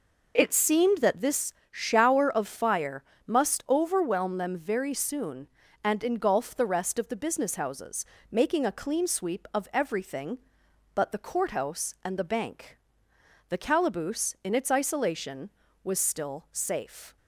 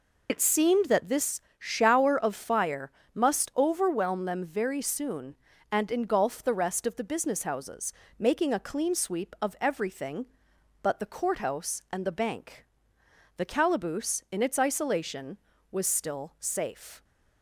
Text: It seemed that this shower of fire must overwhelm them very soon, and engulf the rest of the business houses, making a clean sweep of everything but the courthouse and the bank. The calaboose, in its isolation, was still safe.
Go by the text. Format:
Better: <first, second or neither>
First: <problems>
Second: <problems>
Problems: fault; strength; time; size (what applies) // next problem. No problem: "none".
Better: first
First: pauses between "this" and "shower"; slight; at 1.5 s; 0.18 s long // pauses between "fire" and "must"; slight; at 3.0 s; 0.24 s long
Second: loses the start of "It"; at 0.2 s; 70 ms // pauses between "this" and "shower"; slight; at 1.4 s; 0.18 s long // pauses between "fire" and "must"; slight; at 2.8 s; 0.24 s long